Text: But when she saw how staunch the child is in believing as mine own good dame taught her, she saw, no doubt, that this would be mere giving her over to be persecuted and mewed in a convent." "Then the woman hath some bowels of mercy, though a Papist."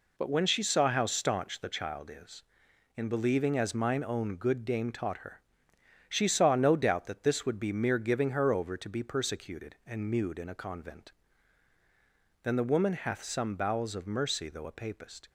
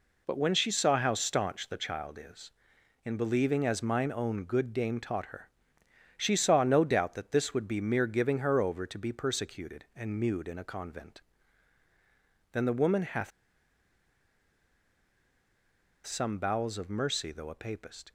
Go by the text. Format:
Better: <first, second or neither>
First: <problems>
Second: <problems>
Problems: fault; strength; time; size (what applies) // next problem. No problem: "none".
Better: first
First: none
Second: pauses between "hath" and "some"; strong; at 13.3 s; 2.7 s long